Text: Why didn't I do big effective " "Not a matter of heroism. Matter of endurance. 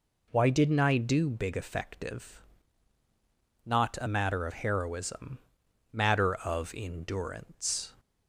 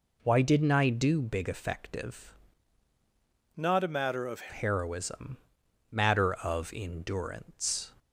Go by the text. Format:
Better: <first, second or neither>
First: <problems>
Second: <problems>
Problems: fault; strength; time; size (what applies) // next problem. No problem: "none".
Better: first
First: none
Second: changes voice from "Not" to "of"; from 3.5 to 4.5 s; 1.0 s long